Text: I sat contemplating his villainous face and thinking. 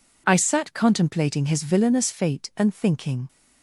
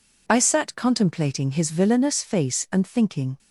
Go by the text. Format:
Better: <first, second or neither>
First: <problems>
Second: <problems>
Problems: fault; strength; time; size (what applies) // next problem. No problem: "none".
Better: second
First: says "fate" for "face"; at 2.0 s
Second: none